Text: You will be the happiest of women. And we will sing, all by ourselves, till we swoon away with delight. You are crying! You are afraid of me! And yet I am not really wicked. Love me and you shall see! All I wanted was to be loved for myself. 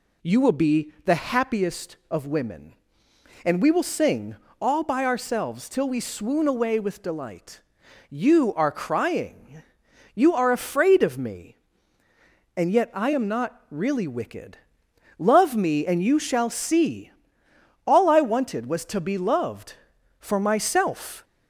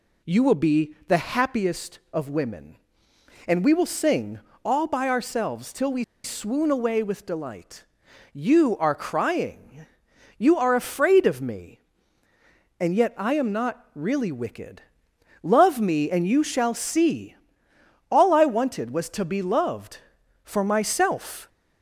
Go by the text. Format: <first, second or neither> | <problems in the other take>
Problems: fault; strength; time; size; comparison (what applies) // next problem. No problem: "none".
first | pauses between "we" and "swoon"; slight; at 6.0 s; 0.19 s long